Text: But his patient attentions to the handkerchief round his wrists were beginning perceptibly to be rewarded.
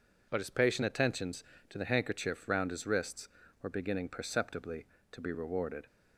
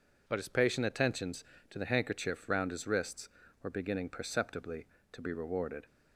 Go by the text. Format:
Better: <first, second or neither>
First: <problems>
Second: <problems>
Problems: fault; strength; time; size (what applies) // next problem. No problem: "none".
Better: neither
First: none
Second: none